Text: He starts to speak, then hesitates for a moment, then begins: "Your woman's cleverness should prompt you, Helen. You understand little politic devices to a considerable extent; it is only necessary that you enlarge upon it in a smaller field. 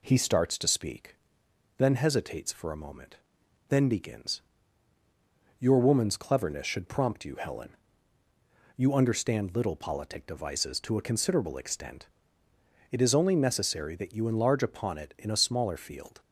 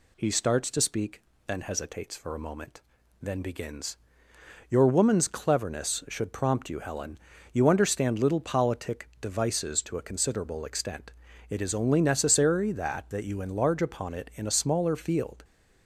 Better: first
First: none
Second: says "that" twice; at 13.0 s

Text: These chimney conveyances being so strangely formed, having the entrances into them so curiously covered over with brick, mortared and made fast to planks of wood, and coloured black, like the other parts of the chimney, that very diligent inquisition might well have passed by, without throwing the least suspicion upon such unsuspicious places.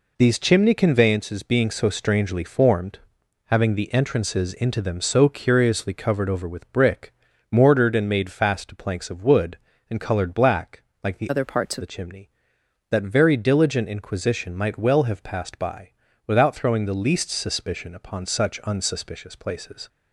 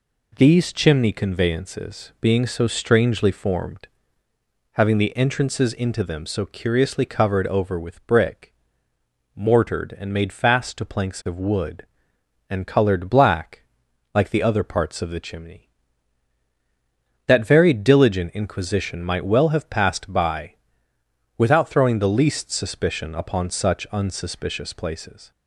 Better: second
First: changes voice from "other" to "of"; from 11.2 to 11.8 s; 0.6 s long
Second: none

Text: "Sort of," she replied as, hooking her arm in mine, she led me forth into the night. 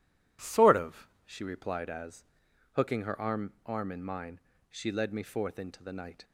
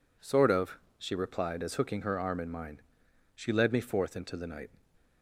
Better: second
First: says "arm" twice; at 3.6 s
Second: none

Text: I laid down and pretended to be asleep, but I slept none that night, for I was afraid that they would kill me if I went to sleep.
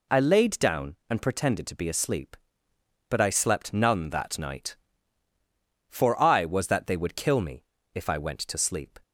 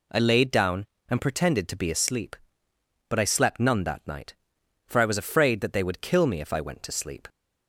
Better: second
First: skips "afraid"; at 6.6 s // pauses between "me" and "if"; slight; at 7.6 s; 0.28 s long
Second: none

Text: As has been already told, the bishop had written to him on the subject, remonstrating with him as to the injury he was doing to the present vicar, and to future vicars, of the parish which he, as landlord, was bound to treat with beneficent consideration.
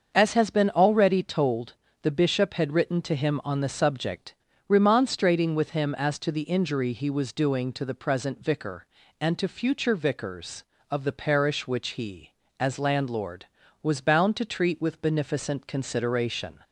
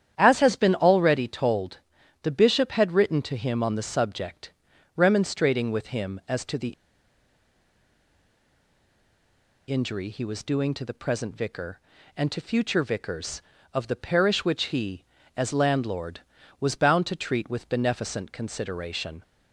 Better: first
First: starts louder than the rest; until 1.1 s; 6.5 dB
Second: starts louder than the rest; strong; until 1.1 s; 10 dB // pauses between "the" and "injury"; strong; at 6.7 s; 2.9 s long

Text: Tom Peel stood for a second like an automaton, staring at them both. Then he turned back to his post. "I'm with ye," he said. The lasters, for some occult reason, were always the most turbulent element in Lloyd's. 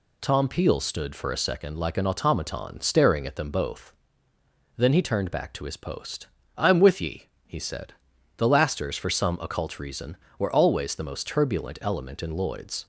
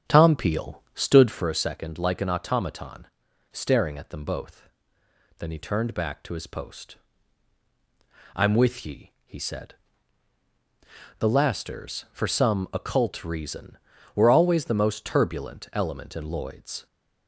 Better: first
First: none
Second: starts louder than the rest; strong; until 1.5 s; 8 dB

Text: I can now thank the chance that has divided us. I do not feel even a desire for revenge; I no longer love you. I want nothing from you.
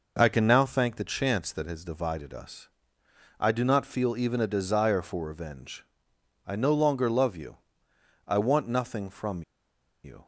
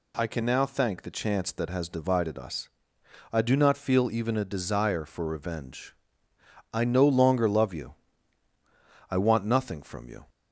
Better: second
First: pauses between "from" and "you"; noticeable; at 9.4 s; 0.60 s long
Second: none

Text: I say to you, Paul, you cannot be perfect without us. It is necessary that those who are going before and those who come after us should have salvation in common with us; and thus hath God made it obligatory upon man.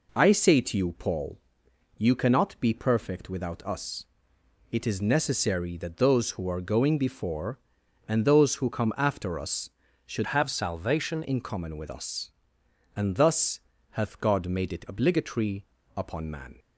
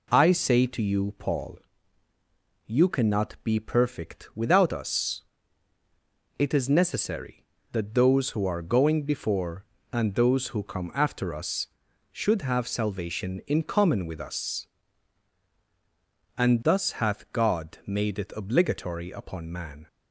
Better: second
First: changes voice from "have" to "salvation"; from 10.2 to 11.2 s; 1.0 s long // pauses between "thus" and "hath"; slight; at 13.5 s; 0.32 s long // pauses between "obligatory" and "upon"; slight; at 15.6 s; 0.32 s long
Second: none

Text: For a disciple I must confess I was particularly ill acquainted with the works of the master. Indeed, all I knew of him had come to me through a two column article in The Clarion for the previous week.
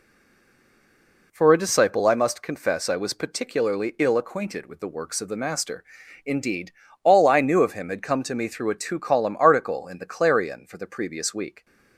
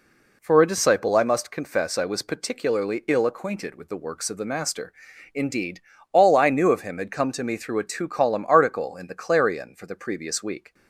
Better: second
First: stays silent before the first word; noticeable; until 1.3 s; 1.3 s long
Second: none

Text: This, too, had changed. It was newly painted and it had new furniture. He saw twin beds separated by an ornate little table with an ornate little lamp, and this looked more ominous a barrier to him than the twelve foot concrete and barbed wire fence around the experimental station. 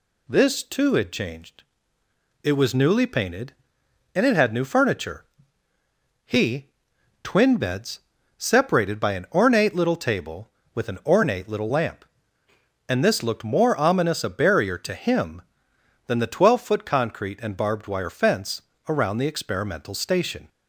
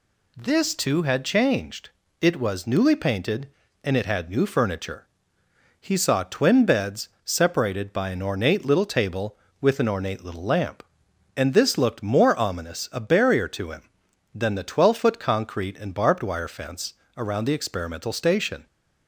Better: second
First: skips "saw"; at 6.9 s // pauses between "beds" and "separated"; slight; at 7.9 s; 0.36 s long // pauses between "fence" and "around"; slight; at 18.6 s; 0.26 s long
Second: pauses between "beds" and "separated"; slight; at 7.0 s; 0.16 s long // pauses between "fence" and "around"; slight; at 16.9 s; 0.24 s long

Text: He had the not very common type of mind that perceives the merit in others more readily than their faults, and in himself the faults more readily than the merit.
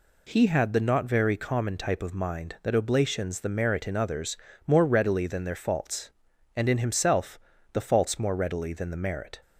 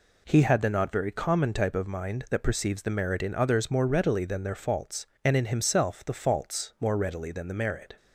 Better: second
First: says "oblations" for "perceives"; at 2.7 s // pauses between "others" and "more"; slight; at 4.3 s; 0.30 s long // pauses between "himself" and "the"; slight; at 7.3 s; 0.32 s long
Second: none

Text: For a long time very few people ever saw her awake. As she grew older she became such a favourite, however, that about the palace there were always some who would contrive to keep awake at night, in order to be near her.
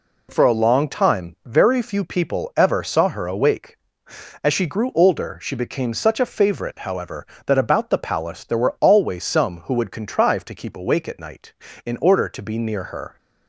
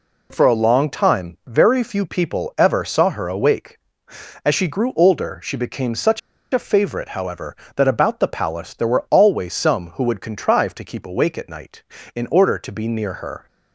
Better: first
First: none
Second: pauses between "such" and "a"; slight; at 6.1 s; 0.33 s long

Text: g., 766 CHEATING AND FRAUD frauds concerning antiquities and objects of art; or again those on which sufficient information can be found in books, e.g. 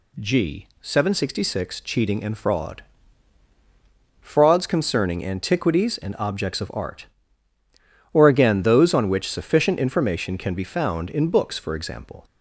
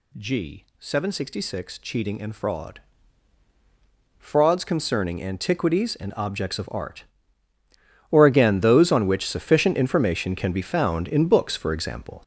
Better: first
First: pauses between "FRAUD" and "frauds"; strong; at 2.8 s; 1.3 s long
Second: gets louder; strong; throughout; 7.5 dB // pauses between "FRAUD" and "frauds"; strong; at 2.8 s; 1.3 s long

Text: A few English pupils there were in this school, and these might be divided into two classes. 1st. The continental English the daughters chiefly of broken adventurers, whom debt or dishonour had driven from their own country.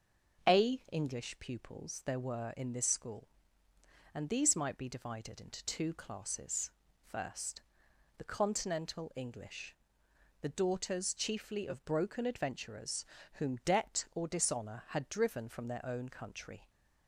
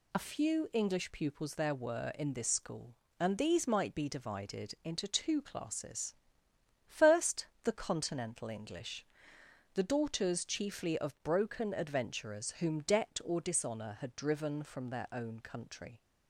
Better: second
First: starts louder than the rest; until 1.5 s; 6.5 dB // skips "few"; at 0.8 s // pauses between "English" and "the"; noticeable; at 9.7 s; 0.66 s long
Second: pauses between "English" and "the"; noticeable; at 9.0 s; 0.70 s long

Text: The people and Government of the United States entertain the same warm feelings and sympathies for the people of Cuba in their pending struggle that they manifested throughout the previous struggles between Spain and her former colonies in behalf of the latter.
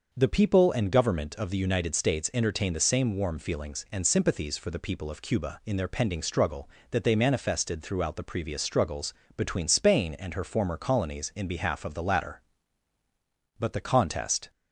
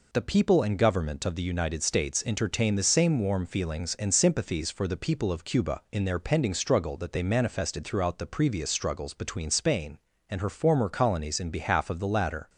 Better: second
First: pauses between "struggles" and "between"; slight; at 9.1 s; 0.24 s long // goes on to say "But the contest"; noticeable; from 13.5 s on; 0.92 s long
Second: none

